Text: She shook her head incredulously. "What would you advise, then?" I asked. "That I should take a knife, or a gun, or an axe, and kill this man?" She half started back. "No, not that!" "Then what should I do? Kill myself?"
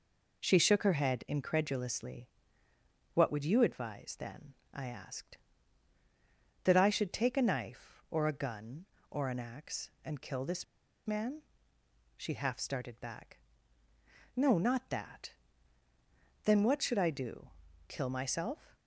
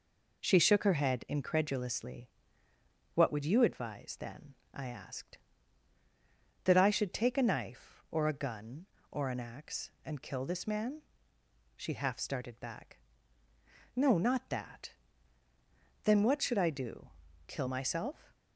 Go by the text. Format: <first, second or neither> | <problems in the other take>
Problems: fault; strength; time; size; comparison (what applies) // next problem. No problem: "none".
second | pauses between "this" and "man"; at 10.6 s; 0.41 s long